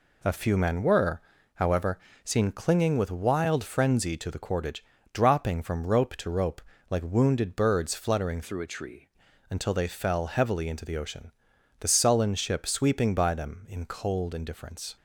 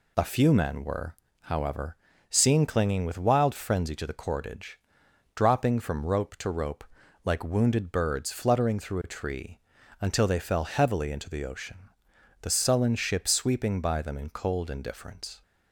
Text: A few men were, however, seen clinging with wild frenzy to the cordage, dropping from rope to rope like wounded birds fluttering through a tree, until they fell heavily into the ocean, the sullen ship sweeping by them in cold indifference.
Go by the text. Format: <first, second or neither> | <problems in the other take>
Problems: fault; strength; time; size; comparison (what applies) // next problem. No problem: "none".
second | pauses between "rope" and "like"; slight; at 6.6 s; 0.30 s long; also in the second // changes voice from "through" to "tree"; from 8.4 to 9.0 s; 0.6 s long